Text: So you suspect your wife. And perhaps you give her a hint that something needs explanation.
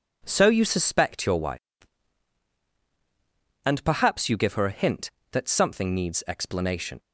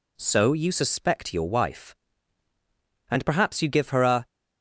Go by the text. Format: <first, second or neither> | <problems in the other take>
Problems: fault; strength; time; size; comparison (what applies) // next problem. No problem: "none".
first | stops before "hint that something needs explanation"; at 4.2 s